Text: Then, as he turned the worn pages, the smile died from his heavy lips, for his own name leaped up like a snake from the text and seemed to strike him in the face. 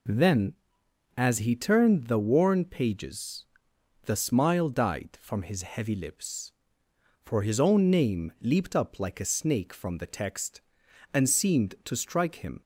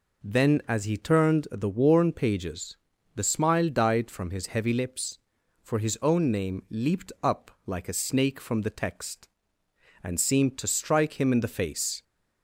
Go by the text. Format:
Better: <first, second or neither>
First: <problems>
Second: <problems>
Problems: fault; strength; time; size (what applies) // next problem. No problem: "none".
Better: second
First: stops before "in the face"; at 12.6 s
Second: none